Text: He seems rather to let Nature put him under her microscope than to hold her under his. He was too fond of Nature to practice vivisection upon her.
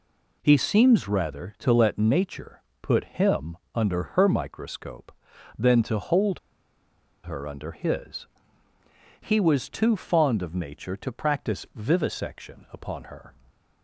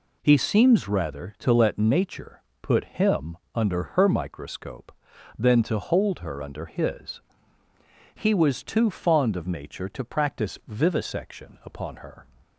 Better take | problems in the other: second | pauses between "Nature" and "put"; slight; at 2.6 s; 0.20 s long; slight in the second // pauses between "him" and "under"; slight; at 3.5 s; 0.16 s long; slight in the second // pauses between "hold" and "her"; noticeable; at 6.3 s; 0.85 s long

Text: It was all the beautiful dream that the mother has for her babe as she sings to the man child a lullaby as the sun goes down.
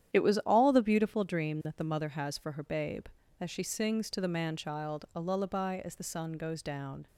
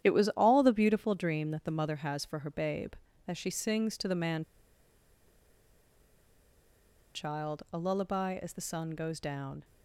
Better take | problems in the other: first | starts louder than the rest; strong; until 1.0 s; 10 dB; strong in the first // pauses between "man" and "child"; strong; at 4.4 s; 2.7 s long

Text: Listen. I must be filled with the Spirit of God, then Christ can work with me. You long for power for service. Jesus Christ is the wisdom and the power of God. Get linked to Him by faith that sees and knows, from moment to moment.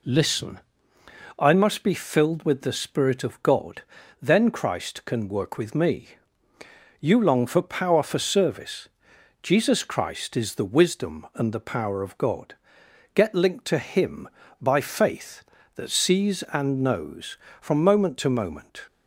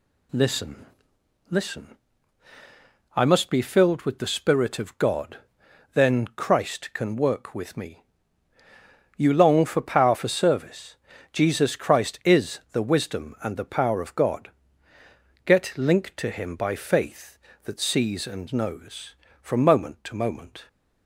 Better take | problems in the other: first | says "Listen" twice; at 1.5 s

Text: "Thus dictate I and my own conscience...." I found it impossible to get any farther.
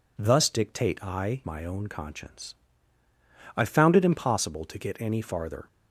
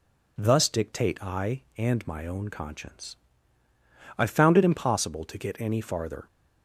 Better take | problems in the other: second | skips "and"; at 1.4 s

